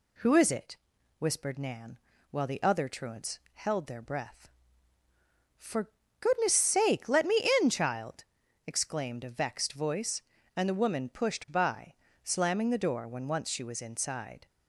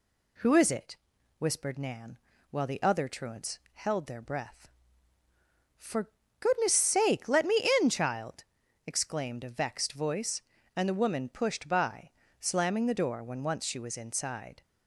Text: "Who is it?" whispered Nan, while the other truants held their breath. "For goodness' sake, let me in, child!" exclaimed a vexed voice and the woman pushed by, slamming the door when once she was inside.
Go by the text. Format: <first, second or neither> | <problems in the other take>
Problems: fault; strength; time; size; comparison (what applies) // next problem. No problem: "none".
neither | pauses between "For" and "goodness"; slight; the same in both